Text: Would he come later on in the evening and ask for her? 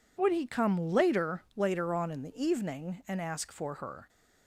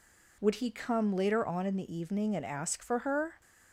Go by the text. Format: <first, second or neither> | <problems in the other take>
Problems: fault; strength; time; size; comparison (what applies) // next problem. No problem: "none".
second | says "later" twice; at 1.5 s